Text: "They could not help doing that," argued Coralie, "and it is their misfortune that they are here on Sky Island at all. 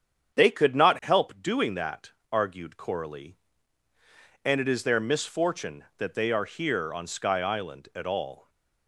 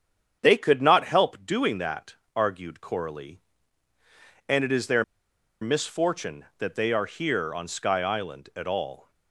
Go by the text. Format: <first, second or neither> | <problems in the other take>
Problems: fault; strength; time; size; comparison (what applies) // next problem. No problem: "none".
first | starts louder than the rest; strong; until 1.4 s; 8 dB; strong in the first // pauses between "their" and "misfortune"; noticeable; at 5.0 s; 0.58 s long